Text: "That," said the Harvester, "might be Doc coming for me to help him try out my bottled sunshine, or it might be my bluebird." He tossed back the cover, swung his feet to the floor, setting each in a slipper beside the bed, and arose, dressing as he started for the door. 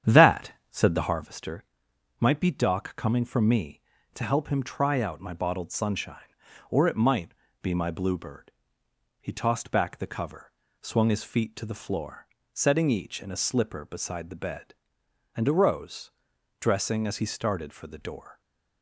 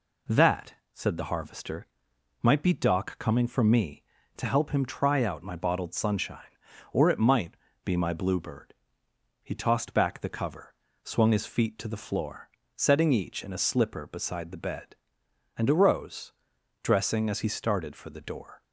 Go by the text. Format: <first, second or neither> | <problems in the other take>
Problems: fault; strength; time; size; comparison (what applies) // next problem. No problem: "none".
second | starts louder than the rest; strong; until 1.2 s; 9 dB // pauses between "might" and "be"; slight; at 7.3 s; 0.30 s long; slight in the second